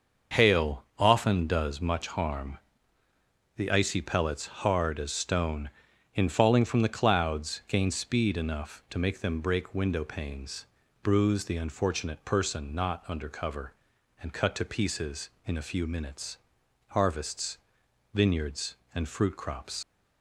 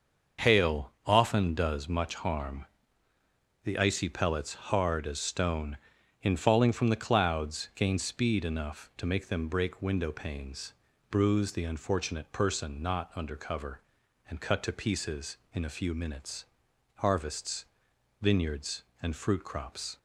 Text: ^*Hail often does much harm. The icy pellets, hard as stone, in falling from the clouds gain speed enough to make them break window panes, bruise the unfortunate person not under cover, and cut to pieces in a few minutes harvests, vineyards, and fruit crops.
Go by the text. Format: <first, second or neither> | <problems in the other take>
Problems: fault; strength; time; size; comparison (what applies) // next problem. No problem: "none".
second | starts louder than the rest; until 1.5 s; 6 dB; also in the second // pauses between "minutes" and "harvests"; noticeable; at 16.3 s; 0.54 s long; noticeable in the second // leaves "crops" unfinished; at 19.8 s; 70 ms